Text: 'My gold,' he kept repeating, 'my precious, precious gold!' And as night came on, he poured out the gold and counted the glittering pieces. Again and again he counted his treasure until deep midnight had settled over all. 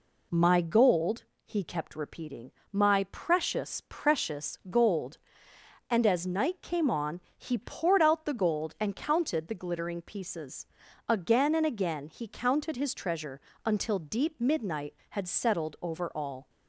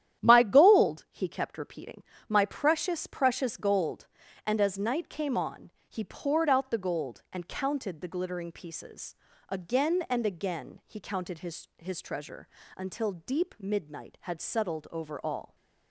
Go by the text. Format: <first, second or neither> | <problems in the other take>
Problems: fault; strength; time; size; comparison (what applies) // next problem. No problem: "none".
first | starts louder than the rest; strong; until 1.2 s; 10.5 dB // says "his" twice; at 11.7 s // pauses between "treasure" and "until"; slight; at 12.4 s; 0.26 s long; slight in the first